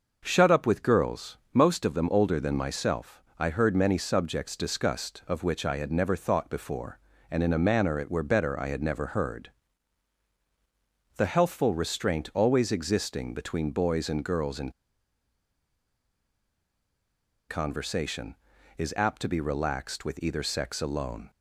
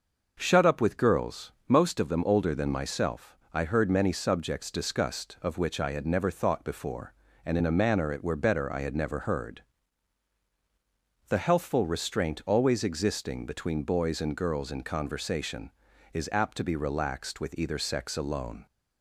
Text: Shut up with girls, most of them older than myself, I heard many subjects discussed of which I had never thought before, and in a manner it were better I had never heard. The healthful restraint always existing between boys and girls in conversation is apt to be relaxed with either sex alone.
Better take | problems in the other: second | pauses between "in" and "conversation"; strong; at 14.6 s; 2.7 s long

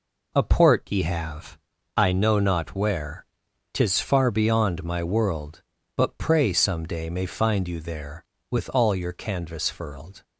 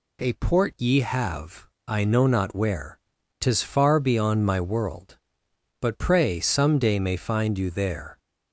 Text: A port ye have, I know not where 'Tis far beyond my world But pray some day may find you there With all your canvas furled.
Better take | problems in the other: first | pauses between "where" and "Tis"; at 2.9 s; 0.42 s long; noticeable in the first // stops before "With all your canvas furled"; at 8.1 s

